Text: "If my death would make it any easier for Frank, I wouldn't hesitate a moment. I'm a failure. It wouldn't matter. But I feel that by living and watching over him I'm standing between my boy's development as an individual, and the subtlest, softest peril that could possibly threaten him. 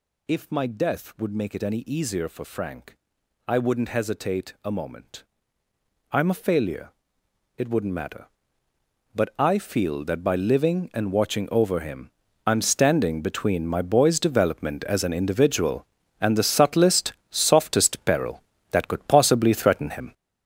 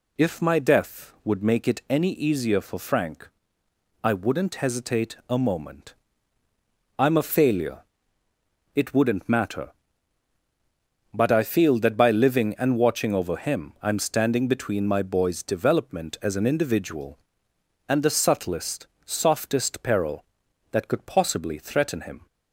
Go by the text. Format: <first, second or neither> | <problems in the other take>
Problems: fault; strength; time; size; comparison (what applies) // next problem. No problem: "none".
second | gets louder; strong; throughout; 7.5 dB // pauses between "him" and "I'm"; slight; at 12.1 s; 0.36 s long